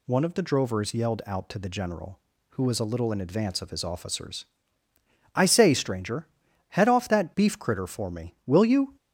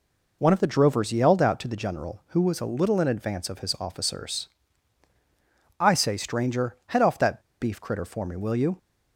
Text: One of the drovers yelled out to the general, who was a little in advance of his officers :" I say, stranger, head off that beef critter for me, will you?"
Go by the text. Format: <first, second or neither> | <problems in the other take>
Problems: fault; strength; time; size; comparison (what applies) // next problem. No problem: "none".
first | pauses between "that" and "beef"; slight; at 7.4 s; 0.18 s long